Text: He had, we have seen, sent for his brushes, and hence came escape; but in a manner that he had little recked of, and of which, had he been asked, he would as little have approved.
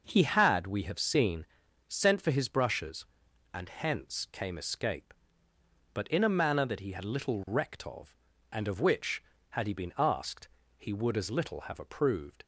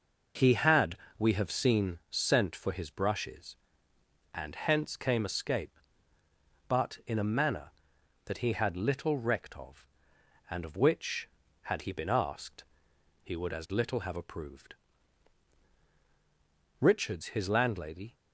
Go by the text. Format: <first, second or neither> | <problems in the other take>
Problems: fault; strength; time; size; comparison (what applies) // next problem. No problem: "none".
first | goes on to say "Richards his landlady"; from 16.7 s on; 1.3 s long